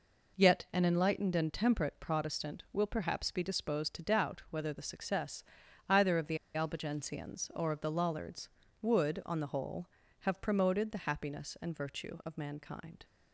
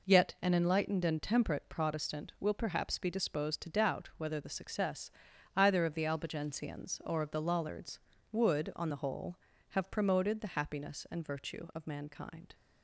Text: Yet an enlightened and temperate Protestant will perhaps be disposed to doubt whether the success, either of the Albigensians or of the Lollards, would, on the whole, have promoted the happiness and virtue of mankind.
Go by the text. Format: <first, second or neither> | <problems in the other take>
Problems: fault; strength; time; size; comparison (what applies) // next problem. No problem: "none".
second | pauses between "the" and "Albigensians"; slight; at 6.3 s; 0.17 s long